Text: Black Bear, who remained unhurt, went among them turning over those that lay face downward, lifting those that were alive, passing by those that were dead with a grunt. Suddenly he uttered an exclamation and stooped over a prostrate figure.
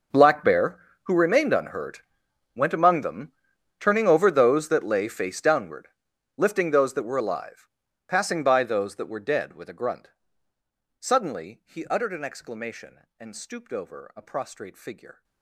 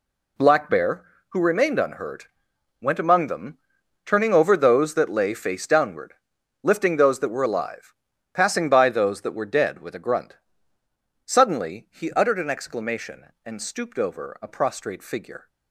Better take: second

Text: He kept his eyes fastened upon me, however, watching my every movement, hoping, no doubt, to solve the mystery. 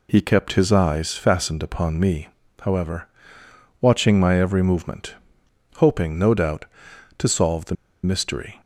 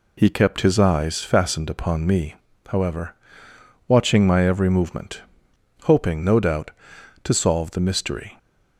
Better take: second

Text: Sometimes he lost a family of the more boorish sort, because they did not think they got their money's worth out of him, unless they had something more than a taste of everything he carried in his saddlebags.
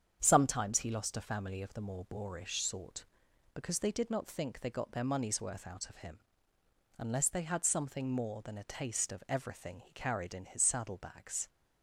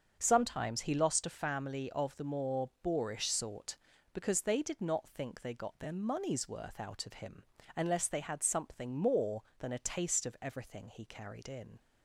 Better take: first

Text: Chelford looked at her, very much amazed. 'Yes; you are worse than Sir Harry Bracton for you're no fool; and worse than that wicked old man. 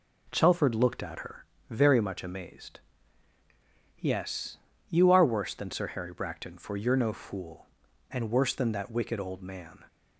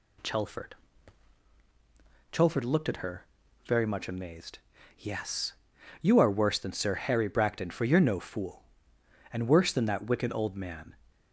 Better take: first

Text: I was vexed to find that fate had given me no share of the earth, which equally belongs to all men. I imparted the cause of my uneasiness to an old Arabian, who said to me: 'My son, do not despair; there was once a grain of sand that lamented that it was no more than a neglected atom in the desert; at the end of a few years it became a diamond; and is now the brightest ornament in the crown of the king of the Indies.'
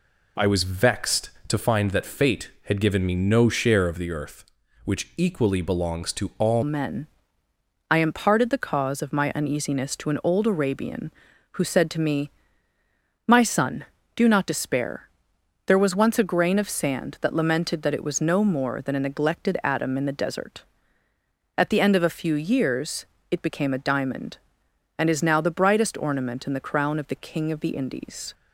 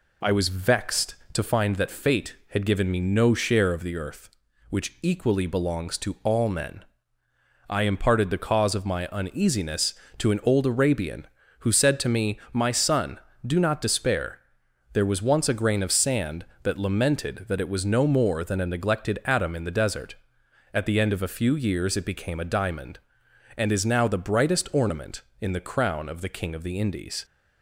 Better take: second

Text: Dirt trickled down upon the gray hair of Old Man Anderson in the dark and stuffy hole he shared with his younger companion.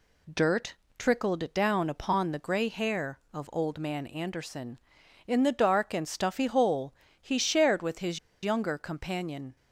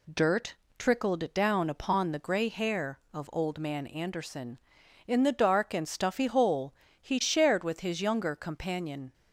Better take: second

